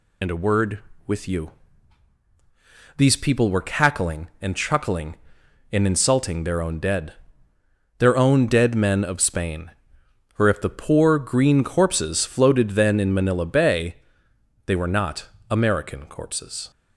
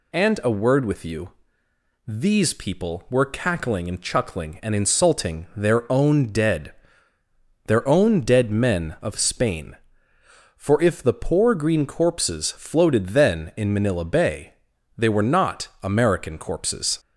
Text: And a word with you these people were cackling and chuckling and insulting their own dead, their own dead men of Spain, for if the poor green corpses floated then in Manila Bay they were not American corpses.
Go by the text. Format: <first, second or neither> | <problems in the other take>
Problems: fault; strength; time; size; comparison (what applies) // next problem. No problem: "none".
second | loses the start of "And"; at 0.2 s; 30 ms // pauses between "you" and "these"; strong; at 1.5 s; 1.4 s long; noticeable in the second // pauses between "Bay" and "they"; noticeable; at 13.9 s; 0.68 s long; also in the second // pauses between "not" and "American"; slight; at 15.2 s; 0.24 s long; slight in the second